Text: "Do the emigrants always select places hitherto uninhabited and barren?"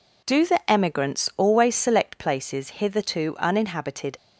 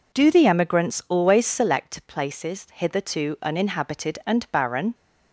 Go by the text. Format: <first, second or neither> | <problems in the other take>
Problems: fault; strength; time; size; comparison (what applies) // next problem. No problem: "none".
second | stops before "and barren"; at 4.1 s